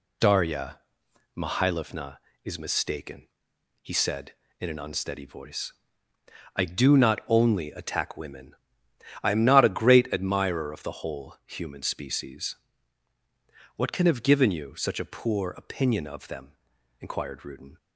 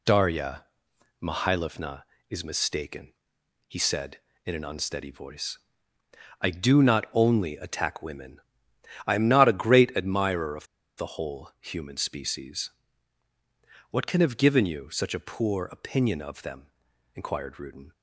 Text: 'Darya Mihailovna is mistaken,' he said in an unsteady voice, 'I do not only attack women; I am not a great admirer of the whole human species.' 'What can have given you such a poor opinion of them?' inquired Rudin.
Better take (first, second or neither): first